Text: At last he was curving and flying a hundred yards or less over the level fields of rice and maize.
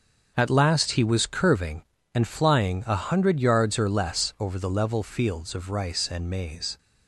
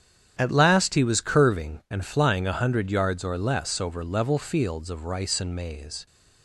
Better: first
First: starts louder than the rest; until 1.3 s; 6.5 dB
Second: starts louder than the rest; strong; until 1.4 s; 9 dB // skips "the"; at 4.0 s

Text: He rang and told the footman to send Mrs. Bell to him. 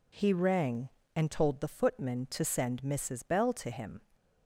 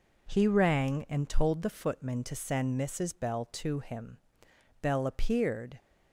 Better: first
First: none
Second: goes on to say "Bell appeared"; noticeable; from 4.8 s on; 0.96 s long

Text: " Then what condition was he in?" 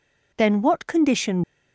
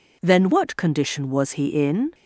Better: second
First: stops before "was he in"; at 1.4 s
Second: none

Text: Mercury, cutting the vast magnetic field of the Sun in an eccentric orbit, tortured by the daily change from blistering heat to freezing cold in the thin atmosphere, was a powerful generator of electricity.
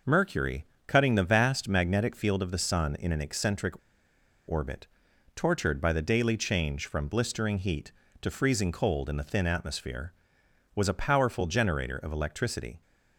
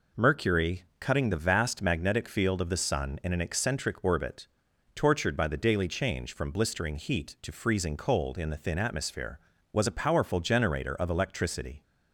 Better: second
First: pauses between "eccentric" and "orbit"; noticeable; at 3.7 s; 0.74 s long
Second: none

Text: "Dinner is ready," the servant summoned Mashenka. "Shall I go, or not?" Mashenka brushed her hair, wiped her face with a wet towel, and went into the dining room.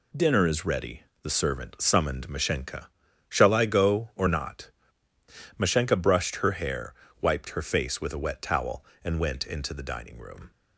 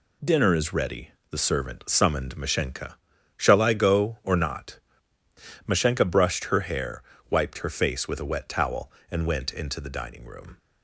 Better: neither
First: none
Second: none

